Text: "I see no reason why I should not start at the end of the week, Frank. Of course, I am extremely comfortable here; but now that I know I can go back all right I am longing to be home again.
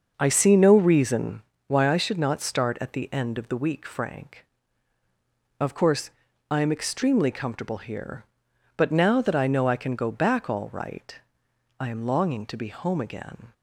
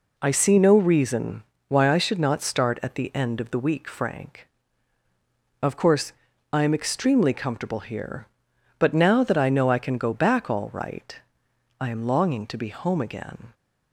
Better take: second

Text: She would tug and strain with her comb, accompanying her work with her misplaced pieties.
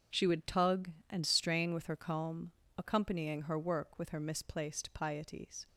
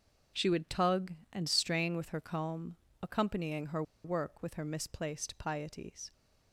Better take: first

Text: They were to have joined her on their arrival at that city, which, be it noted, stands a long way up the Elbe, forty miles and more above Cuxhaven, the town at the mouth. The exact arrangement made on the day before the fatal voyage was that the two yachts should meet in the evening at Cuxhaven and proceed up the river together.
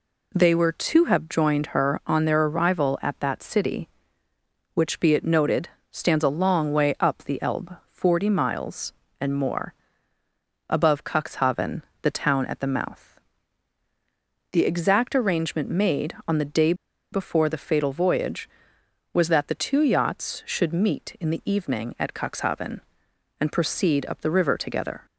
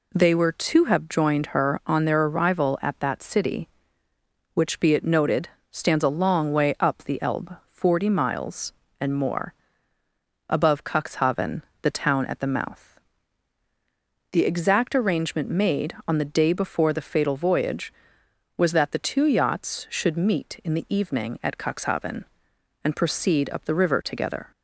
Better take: second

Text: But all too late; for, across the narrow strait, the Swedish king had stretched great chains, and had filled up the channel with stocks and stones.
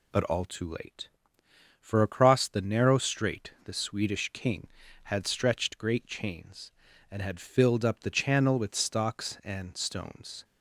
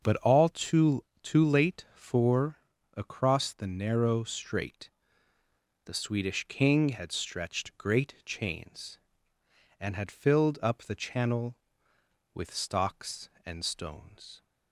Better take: first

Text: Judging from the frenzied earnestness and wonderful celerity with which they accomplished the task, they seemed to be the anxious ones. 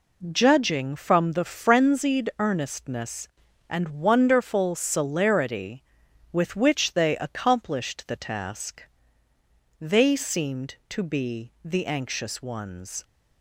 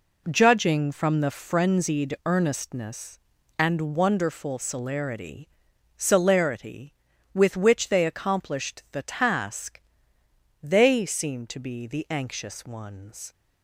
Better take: first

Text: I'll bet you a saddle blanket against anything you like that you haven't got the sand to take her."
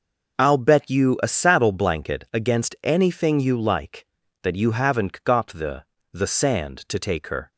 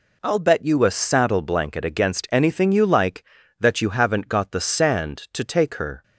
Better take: second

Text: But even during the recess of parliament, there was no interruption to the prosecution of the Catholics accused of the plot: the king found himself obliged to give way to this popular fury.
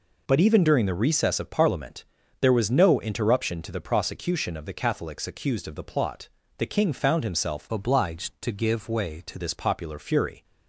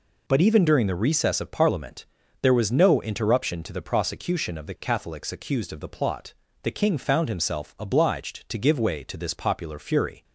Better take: second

